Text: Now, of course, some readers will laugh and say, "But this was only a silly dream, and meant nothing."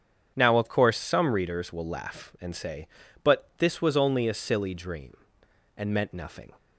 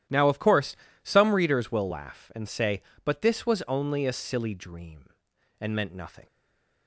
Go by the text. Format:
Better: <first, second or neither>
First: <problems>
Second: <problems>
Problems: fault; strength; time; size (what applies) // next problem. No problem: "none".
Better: first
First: starts louder than the rest; strong; until 1.3 s; 8 dB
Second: starts louder than the rest; strong; until 1.3 s; 12 dB // stays silent after the last word; slight; from 6.2 s on; 0.6 s long